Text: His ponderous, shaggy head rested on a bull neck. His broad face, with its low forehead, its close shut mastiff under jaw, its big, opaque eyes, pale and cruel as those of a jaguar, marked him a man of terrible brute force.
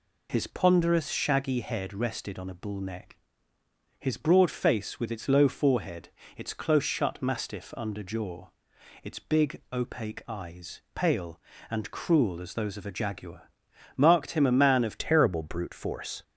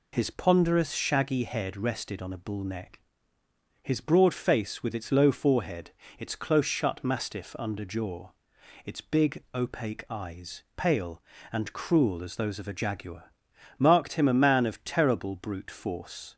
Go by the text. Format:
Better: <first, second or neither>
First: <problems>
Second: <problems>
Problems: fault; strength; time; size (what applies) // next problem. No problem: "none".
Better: second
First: changes voice at "terrible"; from 14.9 s on; 1.3 s long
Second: none